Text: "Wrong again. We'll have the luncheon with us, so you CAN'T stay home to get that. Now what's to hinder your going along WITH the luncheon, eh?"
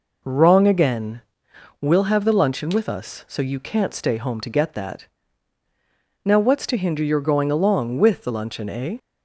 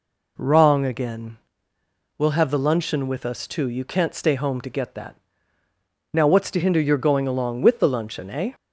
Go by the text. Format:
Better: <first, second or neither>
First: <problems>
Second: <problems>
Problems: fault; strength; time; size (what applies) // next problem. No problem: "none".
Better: first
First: none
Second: says "too" for "so"; at 3.4 s